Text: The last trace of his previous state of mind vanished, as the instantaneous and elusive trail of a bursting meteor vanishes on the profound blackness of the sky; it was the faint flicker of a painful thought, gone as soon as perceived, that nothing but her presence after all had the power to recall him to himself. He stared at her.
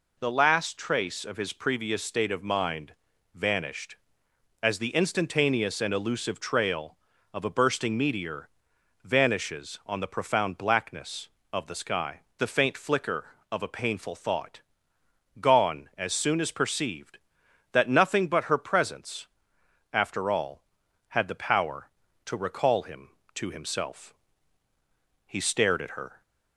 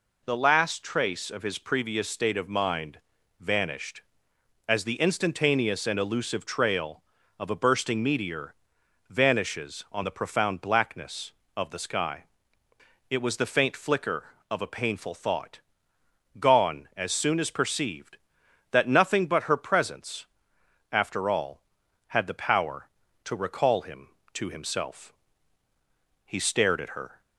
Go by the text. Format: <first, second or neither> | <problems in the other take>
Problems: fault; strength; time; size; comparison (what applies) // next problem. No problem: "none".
second | pauses between "mind" and "vanished"; at 2.9 s; 0.42 s long; also in the second // pauses between "meteor" and "vanishes"; noticeable; at 8.4 s; 0.54 s long; noticeable in the second // skips "it was"; at 12.2 s // pauses between "presence" and "after"; noticeable; at 19.2 s; 0.64 s long; noticeable in the second